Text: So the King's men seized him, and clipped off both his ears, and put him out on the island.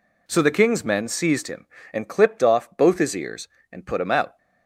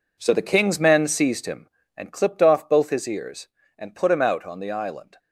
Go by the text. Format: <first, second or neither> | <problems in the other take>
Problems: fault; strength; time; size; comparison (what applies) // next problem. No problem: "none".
second | stops before "on the island"; at 4.3 s